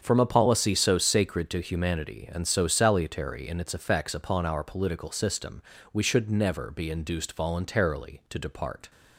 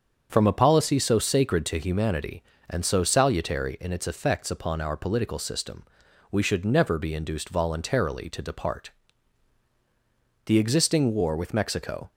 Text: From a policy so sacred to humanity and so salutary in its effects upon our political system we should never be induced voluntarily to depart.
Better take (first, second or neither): first